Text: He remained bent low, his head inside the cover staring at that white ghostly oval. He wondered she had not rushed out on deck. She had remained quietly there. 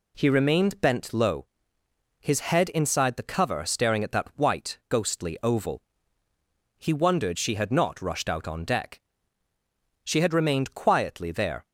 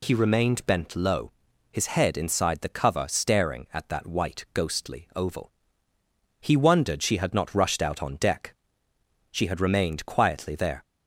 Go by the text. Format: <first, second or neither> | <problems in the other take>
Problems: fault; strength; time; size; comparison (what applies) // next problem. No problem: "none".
neither | none